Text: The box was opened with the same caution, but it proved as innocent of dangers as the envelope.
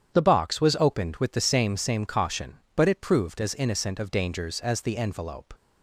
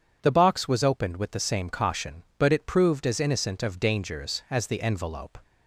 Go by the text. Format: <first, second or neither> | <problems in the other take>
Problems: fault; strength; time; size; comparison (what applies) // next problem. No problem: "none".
second | starts louder than the rest; strong; until 1.1 s; 9 dB // says "same" twice; at 1.7 s